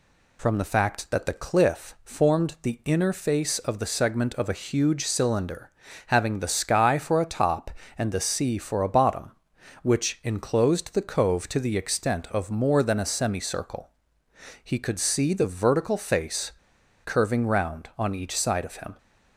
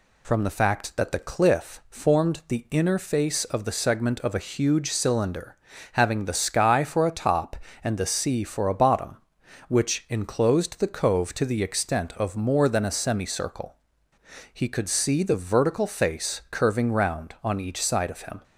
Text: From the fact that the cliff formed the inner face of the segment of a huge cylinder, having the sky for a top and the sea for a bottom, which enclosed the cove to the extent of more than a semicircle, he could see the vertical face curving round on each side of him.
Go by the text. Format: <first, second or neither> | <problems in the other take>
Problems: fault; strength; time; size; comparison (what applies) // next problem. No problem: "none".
second | pauses between "face" and "curving"; noticeable; at 16.5 s; 0.54 s long